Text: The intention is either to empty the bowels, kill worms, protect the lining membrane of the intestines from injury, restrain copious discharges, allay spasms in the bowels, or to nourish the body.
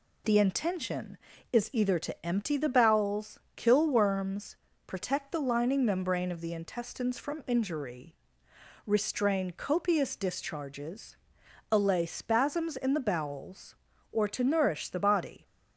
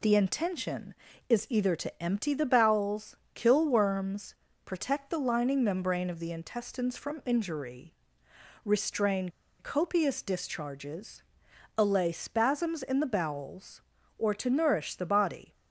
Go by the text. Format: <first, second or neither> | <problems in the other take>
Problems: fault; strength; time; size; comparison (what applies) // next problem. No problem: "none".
first | pauses between "restrain" and "copious"; slight; at 9.3 s; 0.28 s long